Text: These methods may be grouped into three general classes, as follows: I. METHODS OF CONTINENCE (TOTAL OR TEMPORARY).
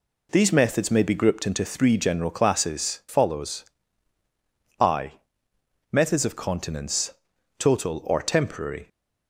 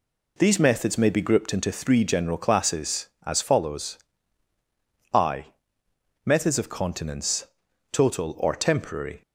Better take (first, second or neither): second